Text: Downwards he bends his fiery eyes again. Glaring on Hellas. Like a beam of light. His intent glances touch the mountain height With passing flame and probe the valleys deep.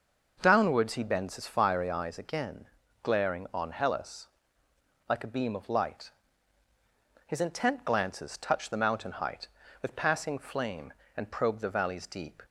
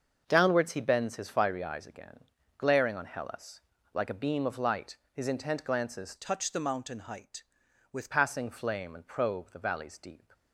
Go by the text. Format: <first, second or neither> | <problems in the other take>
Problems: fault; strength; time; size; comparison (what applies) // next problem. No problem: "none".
first | starts louder than the rest; until 1.2 s; 6.5 dB // changes voice from "touch" to "With"; from 6.1 to 8.1 s; 2.0 s long